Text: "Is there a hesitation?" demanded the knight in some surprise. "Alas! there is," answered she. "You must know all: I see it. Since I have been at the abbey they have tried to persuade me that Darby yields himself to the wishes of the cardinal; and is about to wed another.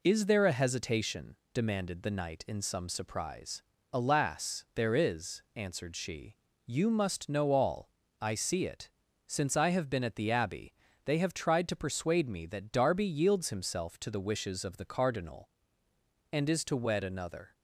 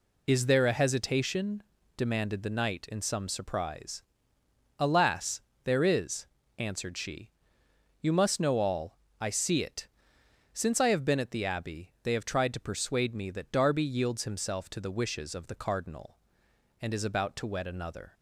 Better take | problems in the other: second | pauses between "abbey" and "they"; slight; at 10.7 s; 0.30 s long // skips "about"; at 16.6 s

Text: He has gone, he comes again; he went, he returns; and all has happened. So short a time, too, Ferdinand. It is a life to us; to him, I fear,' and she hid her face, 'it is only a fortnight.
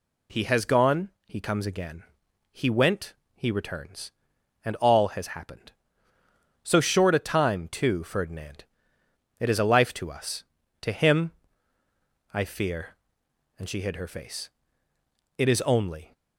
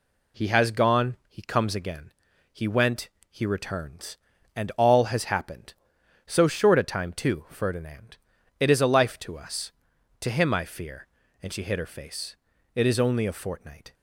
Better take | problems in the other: second | stops before "a fortnight"; at 16.1 s

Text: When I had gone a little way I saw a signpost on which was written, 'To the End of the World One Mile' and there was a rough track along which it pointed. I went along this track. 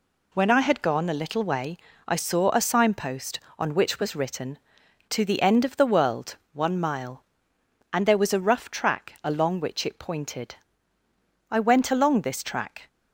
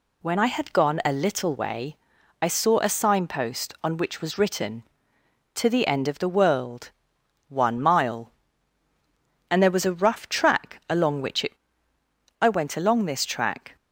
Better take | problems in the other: first | pauses between "way" and "I"; at 1.9 s; 0.44 s long; slight in the first // pauses between "World" and "One"; noticeable; at 6.9 s; 0.56 s long; slight in the first // skips "pointed"; at 11.9 s

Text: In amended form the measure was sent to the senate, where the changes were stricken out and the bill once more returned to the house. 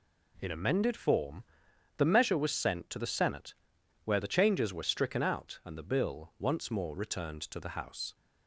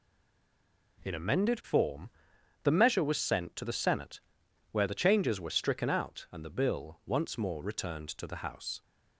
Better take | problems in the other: first | stays silent before the first word; slight; until 0.9 s; 0.9 s long // pauses between "form" and "the"; noticeable; at 2.0 s; 0.52 s long; noticeable in the first

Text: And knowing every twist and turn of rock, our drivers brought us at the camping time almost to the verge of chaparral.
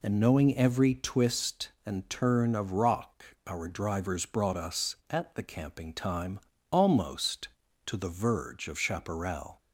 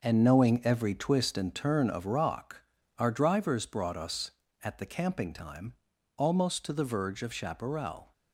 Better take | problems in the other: first | gets quieter; strong; throughout; 8.5 dB // pauses between "time" and "almost"; noticeable; at 5.7 s; 0.46 s long; slight in the first

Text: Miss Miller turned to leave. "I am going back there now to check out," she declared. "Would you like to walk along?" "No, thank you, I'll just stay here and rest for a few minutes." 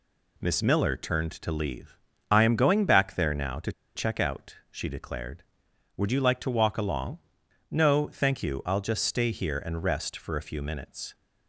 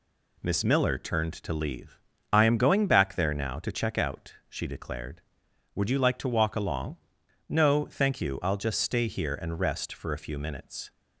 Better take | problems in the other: second | pauses between "to" and "check"; slight; at 3.7 s; 0.24 s long

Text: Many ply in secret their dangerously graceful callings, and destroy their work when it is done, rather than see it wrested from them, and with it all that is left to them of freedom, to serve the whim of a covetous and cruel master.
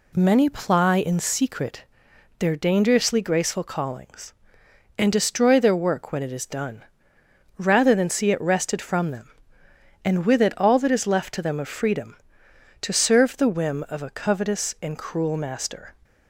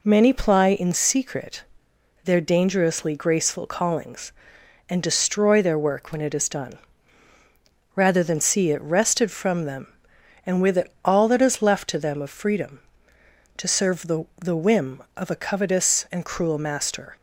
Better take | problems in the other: first | pauses between "secret" and "their"; noticeable; at 1.6 s; 0.60 s long; noticeable in the first // says "the" twice; at 14.3 s

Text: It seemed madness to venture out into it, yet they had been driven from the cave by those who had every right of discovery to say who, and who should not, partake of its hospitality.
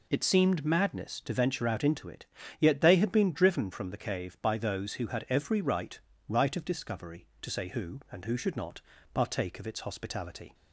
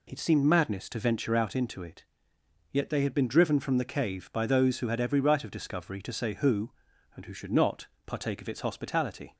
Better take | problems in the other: second | says "right" twice; at 6.2 s

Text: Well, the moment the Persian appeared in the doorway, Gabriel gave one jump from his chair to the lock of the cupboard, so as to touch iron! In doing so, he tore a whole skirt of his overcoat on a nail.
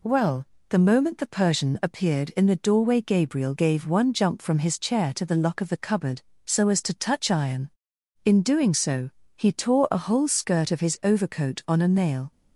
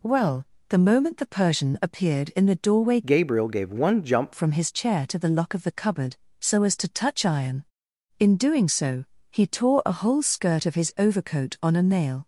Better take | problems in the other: first | changes voice from "Gabriel" to "jump"; from 3.0 to 4.3 s; 1.3 s long

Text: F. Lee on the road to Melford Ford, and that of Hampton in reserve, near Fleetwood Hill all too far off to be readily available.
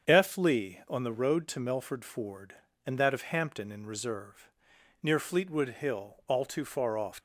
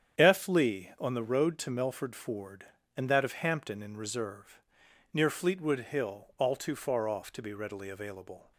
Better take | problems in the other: second | starts louder than the rest; strong; until 1.1 s; 7.5 dB; strong in the second // stops before "to be readily available"; at 7.1 s

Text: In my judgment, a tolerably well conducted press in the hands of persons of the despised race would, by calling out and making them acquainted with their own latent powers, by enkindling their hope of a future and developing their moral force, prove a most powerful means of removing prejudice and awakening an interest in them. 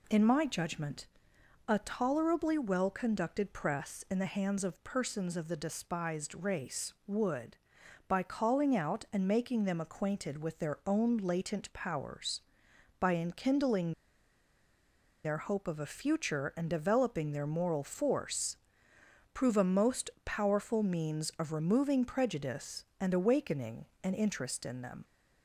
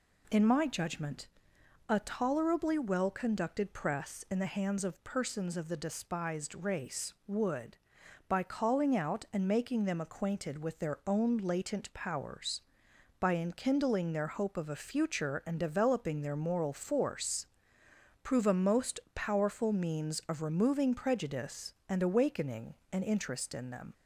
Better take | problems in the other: second | pauses between "enkindling" and "their"; strong; at 13.9 s; 1.3 s long // pauses between "awakening" and "an"; slight; at 23.8 s; 0.20 s long; slight in the second

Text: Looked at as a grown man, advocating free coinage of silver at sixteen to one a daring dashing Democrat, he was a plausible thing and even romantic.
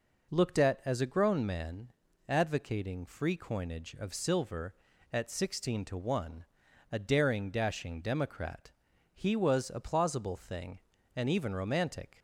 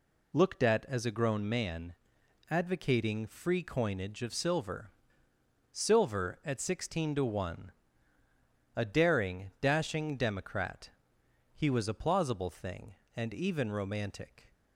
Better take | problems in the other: first | says "silver" twice; at 5.7 s // pauses between "one" and "a"; at 7.7 s; 1.0 s long; noticeable in the first

